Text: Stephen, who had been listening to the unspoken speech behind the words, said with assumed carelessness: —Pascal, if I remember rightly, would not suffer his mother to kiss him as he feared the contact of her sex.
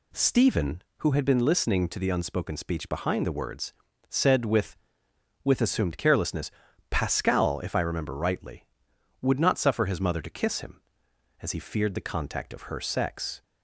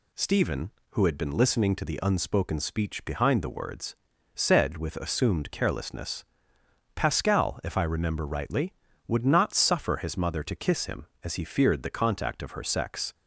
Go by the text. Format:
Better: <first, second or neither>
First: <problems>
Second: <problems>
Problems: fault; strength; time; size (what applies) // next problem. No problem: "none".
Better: second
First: says "with" twice; at 5.4 s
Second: none